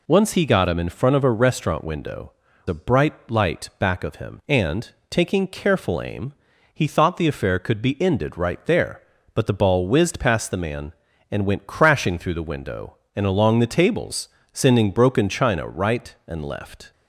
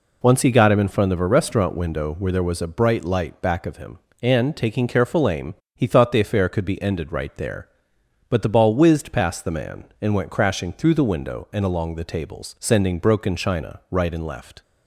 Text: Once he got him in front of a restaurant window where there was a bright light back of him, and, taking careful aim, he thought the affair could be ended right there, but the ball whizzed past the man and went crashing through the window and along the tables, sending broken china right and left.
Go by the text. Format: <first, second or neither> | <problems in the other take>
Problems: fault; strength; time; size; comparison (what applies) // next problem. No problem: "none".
second | skips "where there was"; at 2.5 s // pauses between "bright" and "light"; slight; at 3.1 s; 0.16 s long